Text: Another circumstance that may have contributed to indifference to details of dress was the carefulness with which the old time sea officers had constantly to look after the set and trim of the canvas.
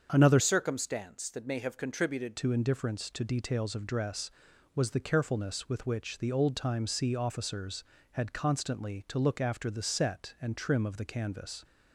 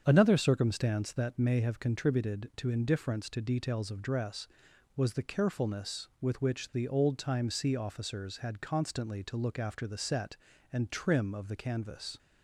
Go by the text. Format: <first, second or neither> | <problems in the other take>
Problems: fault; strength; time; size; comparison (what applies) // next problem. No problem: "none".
second | starts louder than the rest; until 1.1 s; 7 dB; strong in the second // changes voice from "circumstance" to "contributed"; from 0.3 to 2.3 s; 2.0 s long